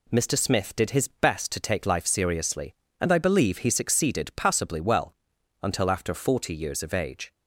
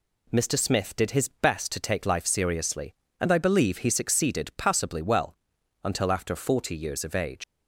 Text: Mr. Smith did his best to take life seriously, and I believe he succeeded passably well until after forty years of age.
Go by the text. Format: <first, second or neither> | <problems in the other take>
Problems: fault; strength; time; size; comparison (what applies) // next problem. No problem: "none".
first | pauses between "well" and "until"; noticeable; at 5.3 s; 0.48 s long; noticeable in the first // leaves "age" unfinished; at 7.4 s; 90 ms